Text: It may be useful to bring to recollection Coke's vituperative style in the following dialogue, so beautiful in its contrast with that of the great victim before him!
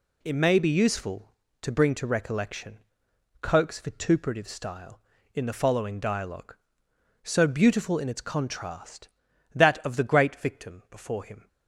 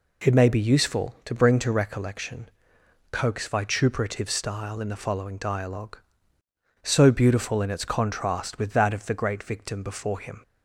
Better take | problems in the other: second | pauses between "recollection" and "Coke's"; noticeable; at 2.8 s; 0.60 s long; noticeable in the second // skips "with"; at 9.3 s

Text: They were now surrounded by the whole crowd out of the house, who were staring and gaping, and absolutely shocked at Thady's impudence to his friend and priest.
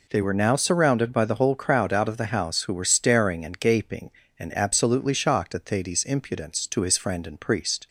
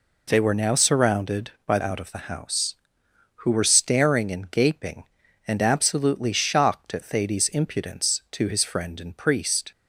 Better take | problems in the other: first | skips "the whole crowd"; at 1.7 s

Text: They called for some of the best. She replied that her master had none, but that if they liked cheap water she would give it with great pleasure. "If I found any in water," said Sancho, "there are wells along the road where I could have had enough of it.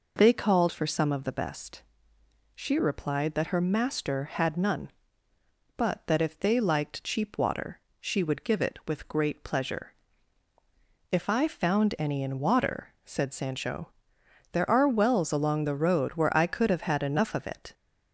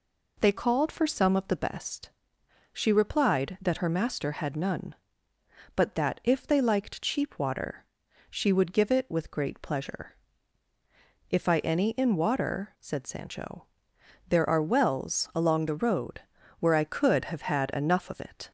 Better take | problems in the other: first | pauses between "water" and "she"; at 7.8 s; 0.44 s long; slight in the first // skips "found"; at 11.5 s // pauses between "road" and "where"; at 16.2 s; 0.38 s long

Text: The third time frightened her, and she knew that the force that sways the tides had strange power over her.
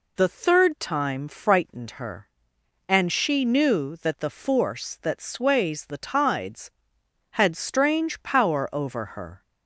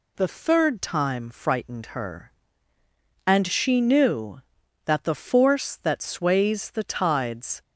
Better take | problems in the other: first | stops before "had strange power over her"; at 7.6 s

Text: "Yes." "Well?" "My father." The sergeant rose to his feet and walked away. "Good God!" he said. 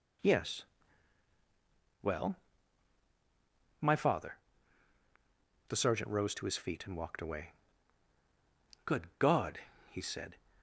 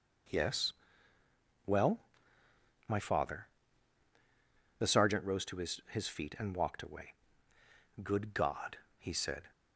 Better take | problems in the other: first | says "his" twice; at 5.8 s

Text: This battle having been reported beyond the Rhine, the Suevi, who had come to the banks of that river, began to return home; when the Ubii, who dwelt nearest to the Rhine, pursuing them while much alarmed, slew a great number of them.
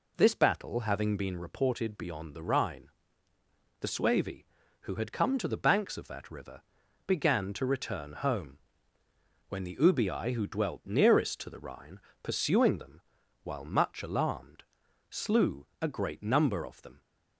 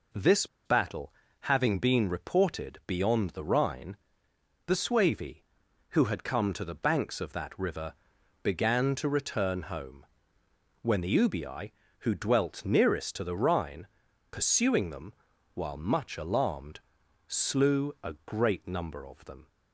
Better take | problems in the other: first | pauses between "This" and "battle"; slight; at 0.4 s; 0.19 s long // pauses between "battle" and "having"; slight; at 1.1 s; 0.30 s long // pauses between "them" and "while"; at 15.1 s; 0.40 s long; also in the first

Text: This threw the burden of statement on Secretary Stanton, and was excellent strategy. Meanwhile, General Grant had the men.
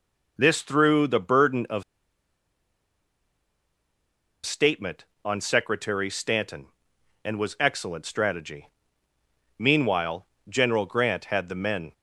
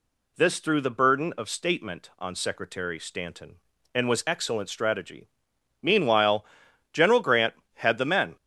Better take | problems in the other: second | pauses between "of" and "statement"; strong; at 1.8 s; 2.6 s long

